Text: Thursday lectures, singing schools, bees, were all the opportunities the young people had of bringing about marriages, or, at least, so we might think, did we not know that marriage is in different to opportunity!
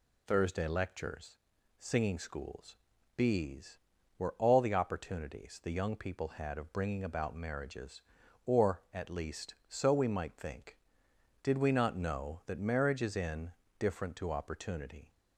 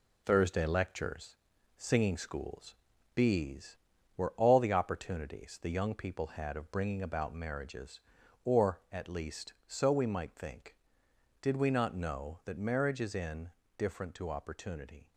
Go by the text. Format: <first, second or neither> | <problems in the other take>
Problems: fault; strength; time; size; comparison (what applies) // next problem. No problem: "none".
first | gets quieter; noticeable; throughout; 6 dB // pauses between "in" and "different"; slight; at 13.5 s; 0.26 s long; slight in the first